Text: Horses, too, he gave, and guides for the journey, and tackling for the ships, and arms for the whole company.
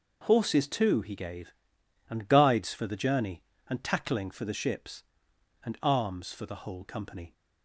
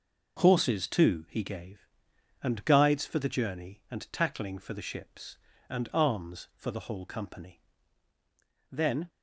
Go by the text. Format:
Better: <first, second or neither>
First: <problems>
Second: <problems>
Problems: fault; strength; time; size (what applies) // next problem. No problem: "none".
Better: first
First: none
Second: goes on to say "Then"; slight; from 8.7 s on; 0.38 s long